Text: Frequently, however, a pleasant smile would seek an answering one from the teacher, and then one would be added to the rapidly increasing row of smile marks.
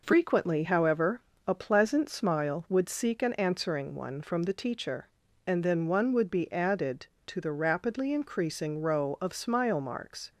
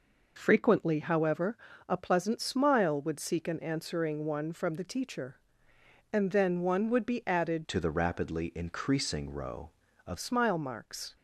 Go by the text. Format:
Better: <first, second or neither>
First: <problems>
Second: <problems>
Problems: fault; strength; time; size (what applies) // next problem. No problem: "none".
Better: first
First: none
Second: changes voice from "to" to "of"; from 7.6 to 10.1 s; 2.5 s long